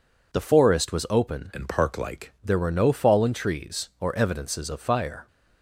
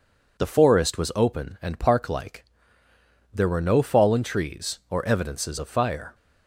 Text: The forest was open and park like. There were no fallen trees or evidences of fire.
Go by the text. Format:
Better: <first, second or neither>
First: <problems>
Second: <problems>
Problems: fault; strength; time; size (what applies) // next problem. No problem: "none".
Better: second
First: changes voice from "and" to "like"; from 1.5 to 2.3 s; 0.8 s long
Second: none